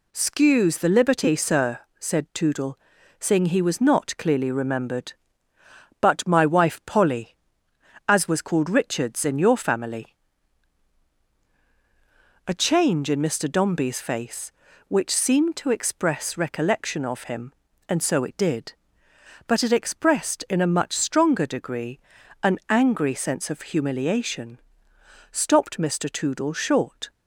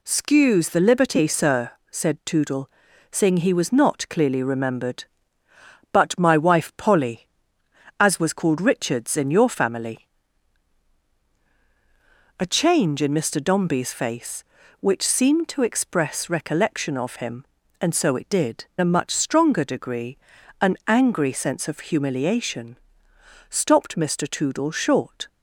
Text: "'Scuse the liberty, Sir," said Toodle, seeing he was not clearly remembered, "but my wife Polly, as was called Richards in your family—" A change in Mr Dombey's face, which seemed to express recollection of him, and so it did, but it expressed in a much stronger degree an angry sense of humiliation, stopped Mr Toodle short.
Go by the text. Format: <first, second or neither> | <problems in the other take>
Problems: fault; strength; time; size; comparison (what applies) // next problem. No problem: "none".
first | skips "but it expressed in"; at 18.7 s // pauses between "degree" and "an"; at 20.1 s; 0.42 s long; also in the first